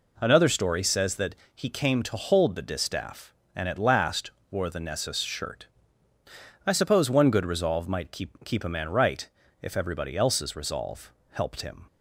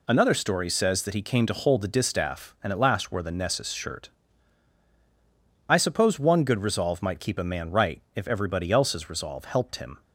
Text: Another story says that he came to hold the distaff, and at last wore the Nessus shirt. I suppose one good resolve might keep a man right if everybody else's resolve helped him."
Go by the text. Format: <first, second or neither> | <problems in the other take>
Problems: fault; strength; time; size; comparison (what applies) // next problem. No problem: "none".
second | pauses between "that" and "he"; slight; at 1.3 s; 0.20 s long // pauses between "last" and "wore"; slight; at 4.3 s; 0.20 s long // says "keep" twice; at 8.4 s // pauses between "right" and "if"; slight; at 9.2 s; 0.34 s long // pauses between "resolve" and "helped"; slight; at 11.1 s; 0.18 s long